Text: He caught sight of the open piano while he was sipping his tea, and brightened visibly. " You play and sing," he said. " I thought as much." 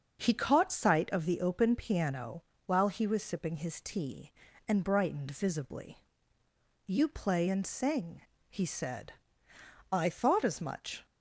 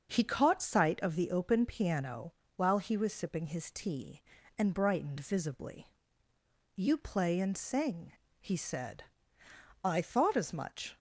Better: neither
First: starts louder than the rest; strong; until 1.2 s; 8.5 dB // pauses between "piano" and "while"; slight; at 2.4 s; 0.24 s long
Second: starts louder than the rest; strong; until 1.1 s; 8.5 dB // pauses between "piano" and "while"; slight; at 2.3 s; 0.24 s long

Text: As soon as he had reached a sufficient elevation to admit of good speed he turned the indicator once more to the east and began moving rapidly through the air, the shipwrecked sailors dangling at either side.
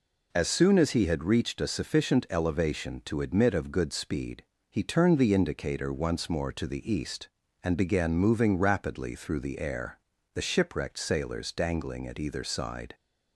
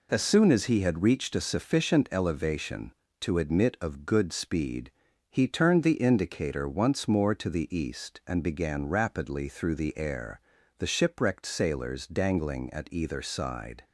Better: first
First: pauses between "speed" and "he"; slight; at 4.4 s; 0.26 s long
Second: pauses between "speed" and "he"; at 4.9 s; 0.40 s long // skips "moving"; at 8.8 s

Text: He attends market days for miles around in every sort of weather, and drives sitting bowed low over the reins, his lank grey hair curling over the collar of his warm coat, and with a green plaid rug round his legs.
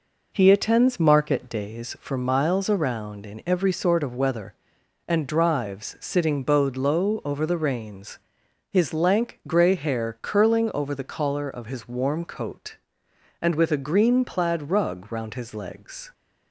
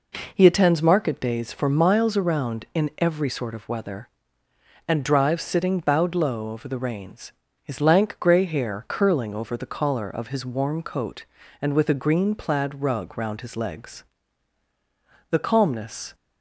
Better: first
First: none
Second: goes on to say "The calmness"; noticeable; from 15.3 s on; 0.84 s long

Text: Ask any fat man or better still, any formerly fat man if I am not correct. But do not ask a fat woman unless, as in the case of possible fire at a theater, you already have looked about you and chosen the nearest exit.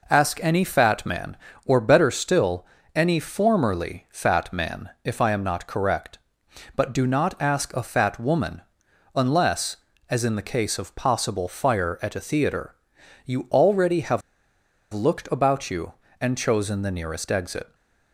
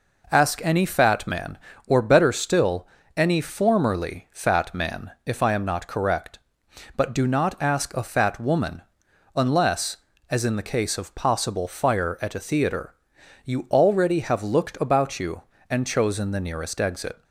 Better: second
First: pauses between "woman" and "unless"; noticeable; at 8.6 s; 0.54 s long // pauses between "have" and "looked"; noticeable; at 14.2 s; 0.73 s long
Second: pauses between "woman" and "unless"; noticeable; at 8.8 s; 0.54 s long

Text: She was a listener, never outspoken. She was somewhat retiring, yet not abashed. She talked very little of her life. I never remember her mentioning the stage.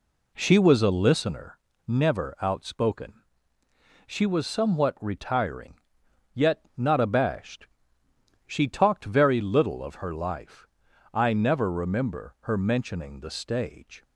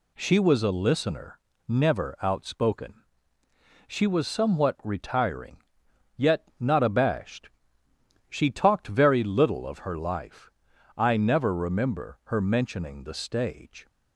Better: second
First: starts louder than the rest; slight; until 1.3 s; 2 dB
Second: none

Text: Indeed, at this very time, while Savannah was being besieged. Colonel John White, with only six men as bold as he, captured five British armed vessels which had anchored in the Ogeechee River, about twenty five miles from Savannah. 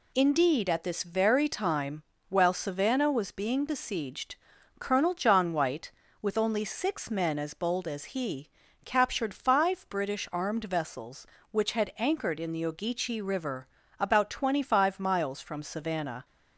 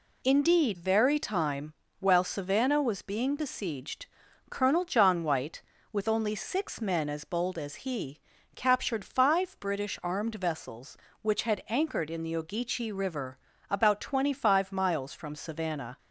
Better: first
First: none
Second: skips "at this"; at 0.7 s

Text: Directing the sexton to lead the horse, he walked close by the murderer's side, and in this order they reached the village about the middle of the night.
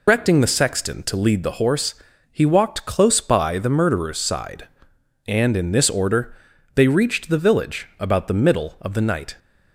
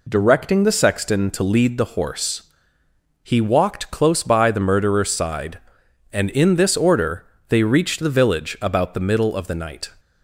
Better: second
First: loses the start of "Directing"; at 0.0 s; 145 ms // pauses between "order" and "they"; at 6.3 s; 0.40 s long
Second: pauses between "order" and "they"; slight; at 7.2 s; 0.24 s long

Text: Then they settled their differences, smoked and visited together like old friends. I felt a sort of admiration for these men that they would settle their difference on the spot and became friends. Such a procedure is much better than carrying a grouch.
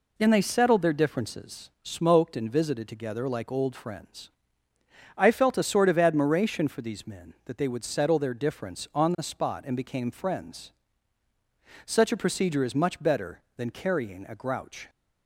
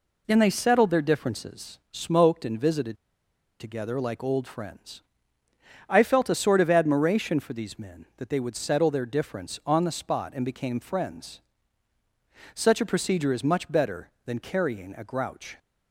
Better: first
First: none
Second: pauses between "visited" and "together"; noticeable; at 2.9 s; 0.63 s long

